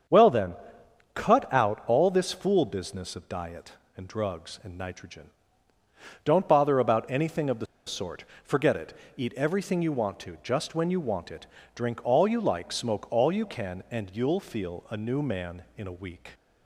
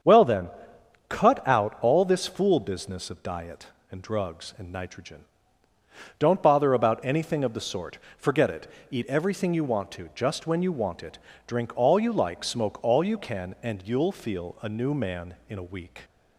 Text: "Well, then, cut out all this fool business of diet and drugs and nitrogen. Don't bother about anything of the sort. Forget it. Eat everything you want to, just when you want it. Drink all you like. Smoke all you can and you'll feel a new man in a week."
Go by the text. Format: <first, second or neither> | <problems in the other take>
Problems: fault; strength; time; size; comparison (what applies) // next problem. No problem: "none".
second | starts louder than the rest; strong; until 1.6 s; 7.5 dB; strong in the second // pauses between "the" and "sort"; slight; at 7.6 s; 0.21 s long